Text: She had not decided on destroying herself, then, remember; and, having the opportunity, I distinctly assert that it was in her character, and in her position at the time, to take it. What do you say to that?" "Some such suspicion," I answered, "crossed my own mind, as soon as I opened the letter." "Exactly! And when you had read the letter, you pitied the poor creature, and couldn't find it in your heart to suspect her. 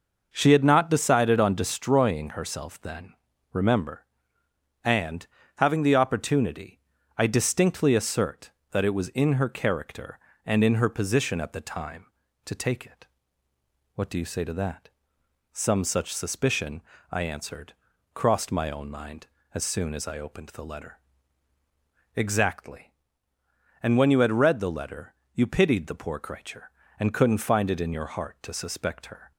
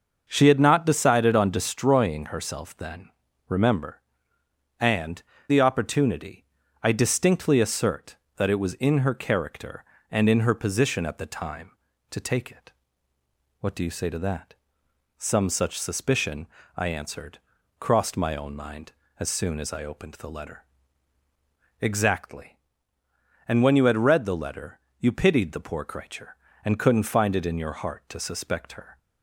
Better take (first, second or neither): first